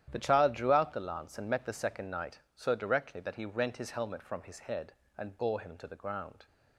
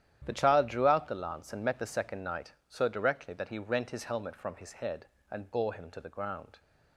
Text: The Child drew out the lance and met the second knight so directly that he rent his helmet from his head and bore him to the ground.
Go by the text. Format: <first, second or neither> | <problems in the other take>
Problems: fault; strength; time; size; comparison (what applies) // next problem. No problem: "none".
neither | starts louder than the rest; strong; the same in both